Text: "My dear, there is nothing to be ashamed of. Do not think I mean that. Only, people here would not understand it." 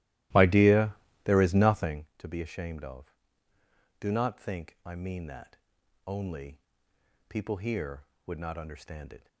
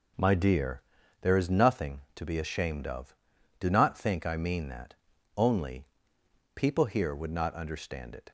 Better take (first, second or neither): second